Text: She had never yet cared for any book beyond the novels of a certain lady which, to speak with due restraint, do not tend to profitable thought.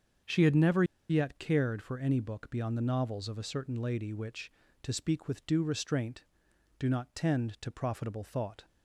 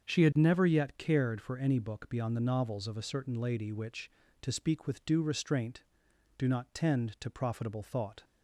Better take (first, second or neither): second